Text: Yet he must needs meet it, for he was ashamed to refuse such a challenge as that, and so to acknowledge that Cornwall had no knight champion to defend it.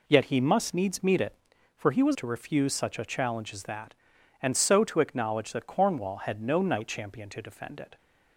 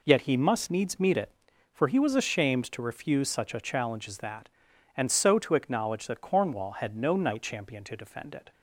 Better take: second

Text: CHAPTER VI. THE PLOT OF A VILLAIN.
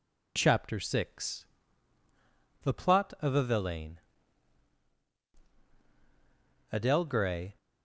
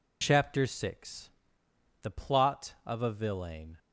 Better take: second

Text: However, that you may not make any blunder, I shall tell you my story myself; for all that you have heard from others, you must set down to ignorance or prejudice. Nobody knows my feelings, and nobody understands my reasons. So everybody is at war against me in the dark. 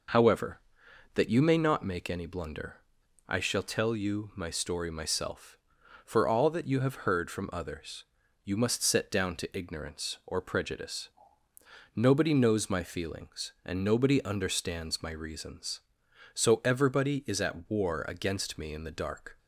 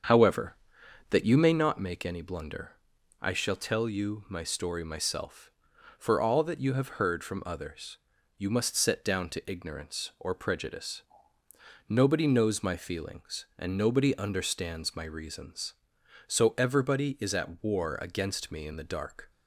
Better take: first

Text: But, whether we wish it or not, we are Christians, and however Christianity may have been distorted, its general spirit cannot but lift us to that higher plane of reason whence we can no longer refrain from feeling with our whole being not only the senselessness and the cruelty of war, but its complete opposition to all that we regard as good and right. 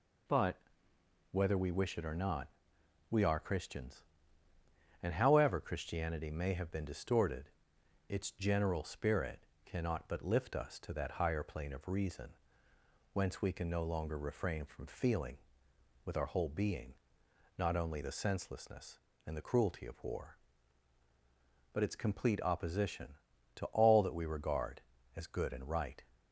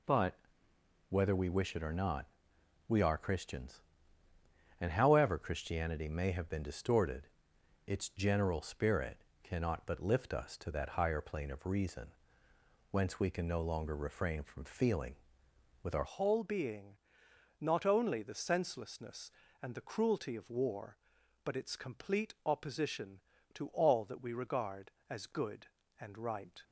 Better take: first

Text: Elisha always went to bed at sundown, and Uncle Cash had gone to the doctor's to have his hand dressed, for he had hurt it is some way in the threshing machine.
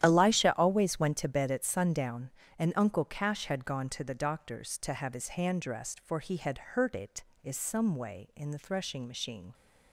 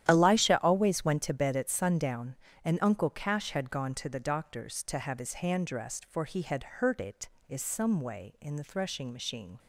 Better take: neither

